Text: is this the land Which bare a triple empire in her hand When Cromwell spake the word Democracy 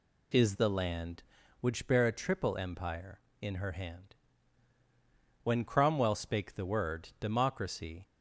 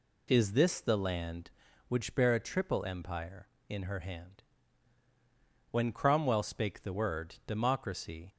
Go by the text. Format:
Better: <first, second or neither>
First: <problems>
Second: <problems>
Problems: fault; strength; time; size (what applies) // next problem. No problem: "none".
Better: second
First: skips "this"; at 0.5 s // pauses between "hand" and "When"; strong; at 4.1 s; 1.2 s long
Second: pauses between "hand" and "When"; strong; at 4.4 s; 1.2 s long